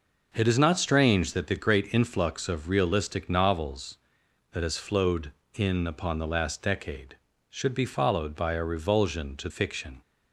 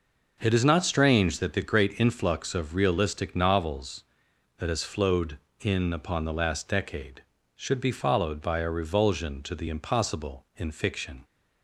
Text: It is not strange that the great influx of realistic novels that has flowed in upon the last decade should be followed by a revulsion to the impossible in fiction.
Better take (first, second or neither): second